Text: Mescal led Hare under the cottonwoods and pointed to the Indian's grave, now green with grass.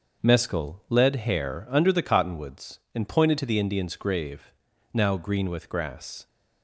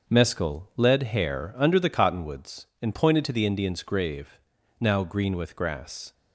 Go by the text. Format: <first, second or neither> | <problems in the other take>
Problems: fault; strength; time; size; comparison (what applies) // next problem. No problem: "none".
neither | starts louder than the rest; the same in both